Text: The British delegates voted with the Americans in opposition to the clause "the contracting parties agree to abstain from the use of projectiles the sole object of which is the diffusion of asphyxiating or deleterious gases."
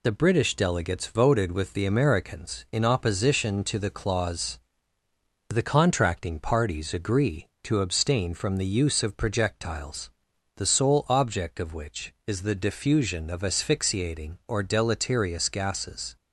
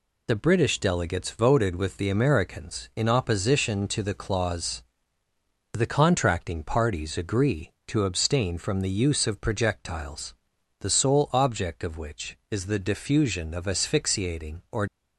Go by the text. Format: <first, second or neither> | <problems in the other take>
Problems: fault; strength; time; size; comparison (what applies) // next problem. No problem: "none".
first | pauses between "clause" and "the"; noticeable; at 4.8 s; 0.88 s long; noticeable in the first // pauses between "projectiles" and "the"; at 10.3 s; 0.42 s long; also in the first // stops before "deleterious gases"; at 14.8 s